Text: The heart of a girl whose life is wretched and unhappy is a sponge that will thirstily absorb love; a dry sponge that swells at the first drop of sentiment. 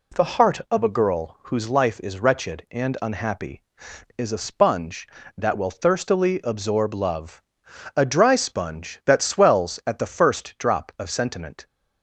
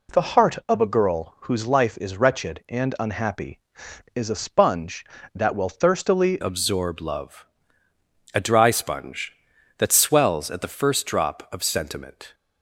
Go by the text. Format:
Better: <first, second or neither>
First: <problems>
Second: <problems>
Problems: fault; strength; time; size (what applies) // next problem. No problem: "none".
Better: first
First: none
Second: changes voice at "absorb"; from 6.4 s on; 5.9 s long